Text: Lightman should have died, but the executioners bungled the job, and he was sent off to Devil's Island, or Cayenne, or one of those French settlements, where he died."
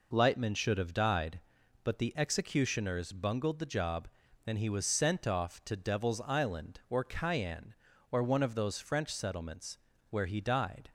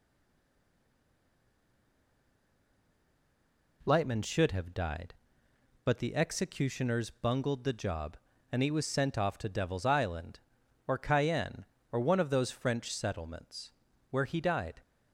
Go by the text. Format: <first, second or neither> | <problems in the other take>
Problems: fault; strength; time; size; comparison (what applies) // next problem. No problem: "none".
first | stays silent before the first word; strong; until 3.8 s; 3.8 s long